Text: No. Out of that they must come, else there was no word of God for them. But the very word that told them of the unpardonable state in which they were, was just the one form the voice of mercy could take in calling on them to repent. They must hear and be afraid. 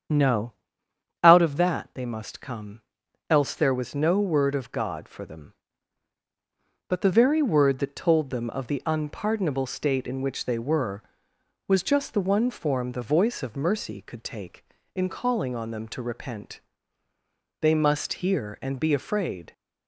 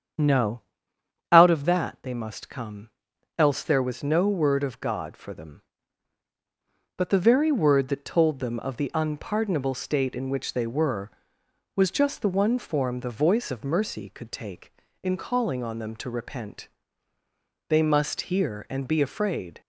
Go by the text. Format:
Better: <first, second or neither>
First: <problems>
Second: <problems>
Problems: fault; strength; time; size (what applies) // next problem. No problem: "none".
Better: neither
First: starts louder than the rest; strong; until 1.8 s; 8 dB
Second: starts louder than the rest; strong; until 1.8 s; 8 dB